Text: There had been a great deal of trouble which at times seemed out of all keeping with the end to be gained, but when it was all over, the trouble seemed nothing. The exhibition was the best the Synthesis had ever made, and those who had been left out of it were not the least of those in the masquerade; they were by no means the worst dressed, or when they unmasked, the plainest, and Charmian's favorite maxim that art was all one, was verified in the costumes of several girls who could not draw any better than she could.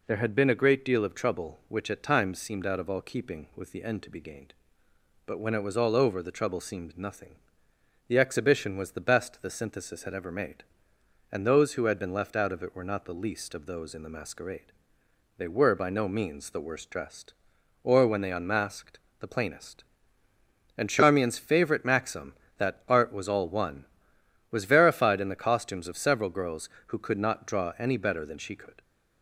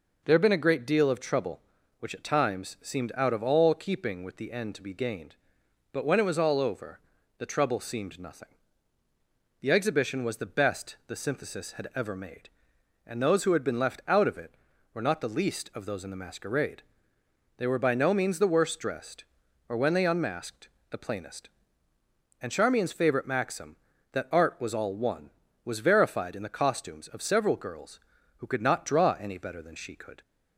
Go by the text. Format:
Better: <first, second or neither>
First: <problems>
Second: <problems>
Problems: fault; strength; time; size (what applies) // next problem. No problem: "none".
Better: neither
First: none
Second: none